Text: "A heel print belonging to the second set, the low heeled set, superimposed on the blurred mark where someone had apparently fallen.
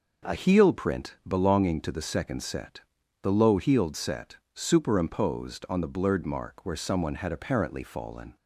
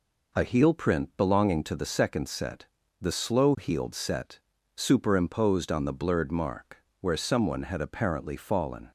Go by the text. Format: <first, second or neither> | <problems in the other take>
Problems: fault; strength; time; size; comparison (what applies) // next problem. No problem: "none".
first | says "slow" for "low"; at 3.1 s // pauses between "mark" and "where"; slight; at 6.8 s; 0.16 s long